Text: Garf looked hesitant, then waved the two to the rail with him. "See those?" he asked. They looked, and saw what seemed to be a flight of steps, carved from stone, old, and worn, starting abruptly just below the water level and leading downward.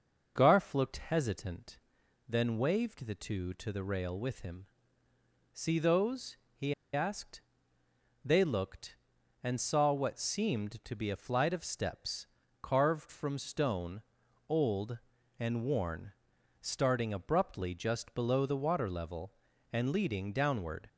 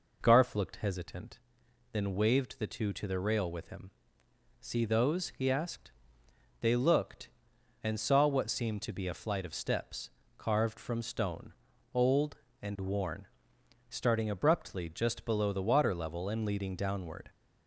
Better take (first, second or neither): second